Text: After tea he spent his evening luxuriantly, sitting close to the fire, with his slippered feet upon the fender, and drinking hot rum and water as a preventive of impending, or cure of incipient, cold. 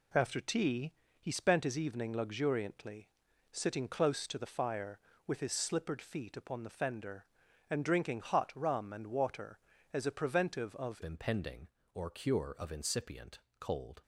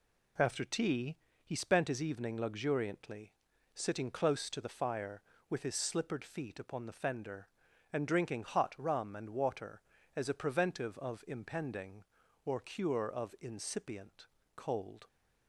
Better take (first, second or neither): second